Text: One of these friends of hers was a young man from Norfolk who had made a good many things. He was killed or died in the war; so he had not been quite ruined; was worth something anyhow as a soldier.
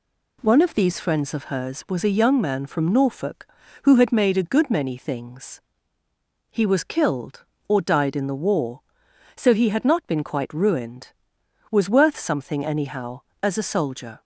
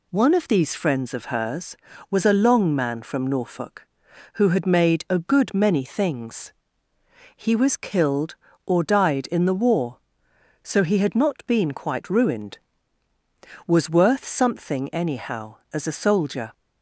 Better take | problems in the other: first | says "long" for "young"; at 2.3 s

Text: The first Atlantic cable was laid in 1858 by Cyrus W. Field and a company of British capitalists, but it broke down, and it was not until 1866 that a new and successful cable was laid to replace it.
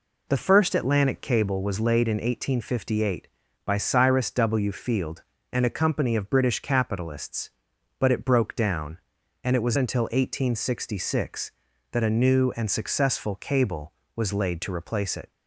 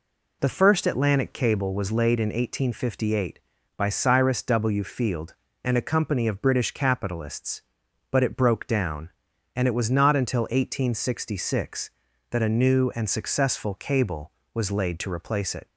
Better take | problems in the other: second | skips "not"; at 9.7 s

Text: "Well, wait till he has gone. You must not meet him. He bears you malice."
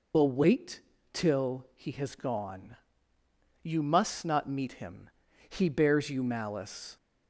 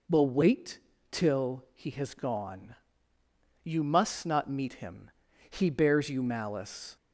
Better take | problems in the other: second | loses the start of "Well"; at 0.1 s; 40 ms // pauses between "wait" and "till"; slight; at 0.8 s; 0.32 s long; slight in the second

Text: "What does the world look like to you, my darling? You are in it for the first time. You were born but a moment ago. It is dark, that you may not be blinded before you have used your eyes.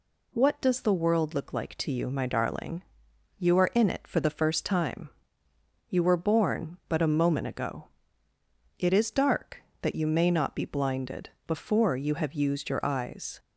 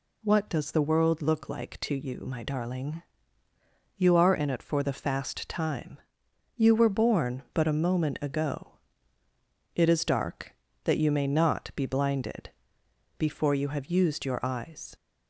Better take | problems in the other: first | says "fast" for "first"; at 4.9 s // pauses between "blinded" and "before"; noticeable; at 12.5 s; 0.66 s long; slight in the first

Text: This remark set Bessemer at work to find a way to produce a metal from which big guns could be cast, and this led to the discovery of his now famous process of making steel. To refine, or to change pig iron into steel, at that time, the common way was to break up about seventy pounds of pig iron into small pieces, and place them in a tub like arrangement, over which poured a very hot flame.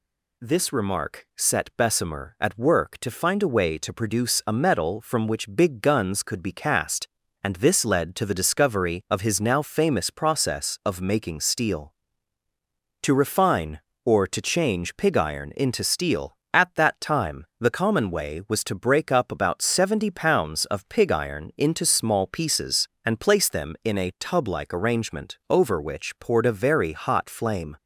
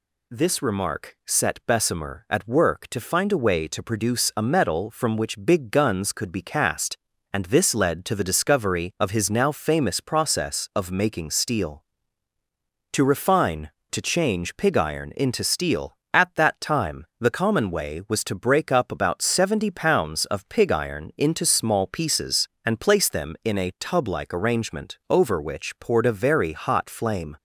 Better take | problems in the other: first | skips "or"; at 13.7 s

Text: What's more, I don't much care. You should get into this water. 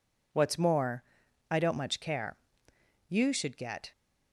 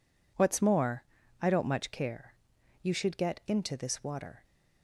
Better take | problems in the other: second | stops before "into this water"; at 3.9 s

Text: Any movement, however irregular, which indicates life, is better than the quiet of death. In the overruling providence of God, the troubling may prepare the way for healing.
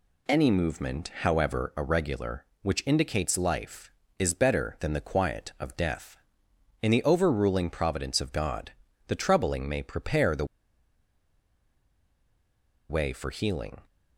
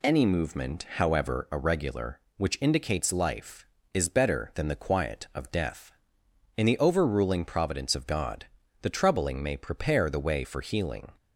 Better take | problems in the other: second | pauses between "the" and "way"; strong; at 10.4 s; 2.4 s long

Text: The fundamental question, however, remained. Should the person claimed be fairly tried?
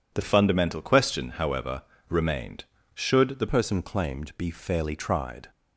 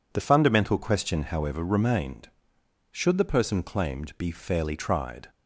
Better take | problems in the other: second | changes voice from "fundamental" to "the"; from 0.2 to 3.4 s; 3.2 s long

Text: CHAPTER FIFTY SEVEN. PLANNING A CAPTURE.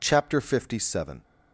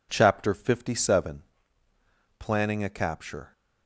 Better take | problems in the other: second | stops before "PLANNING A CAPTURE"; at 1.2 s

